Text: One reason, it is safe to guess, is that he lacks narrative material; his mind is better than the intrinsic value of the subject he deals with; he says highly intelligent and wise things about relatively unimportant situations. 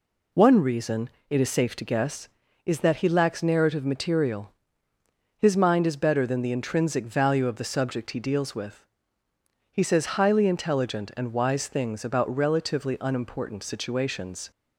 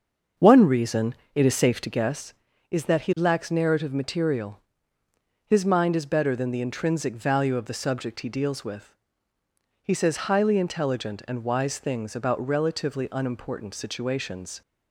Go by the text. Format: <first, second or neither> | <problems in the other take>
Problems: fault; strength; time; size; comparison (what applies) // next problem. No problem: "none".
first | starts louder than the rest; until 2.1 s; 6.5 dB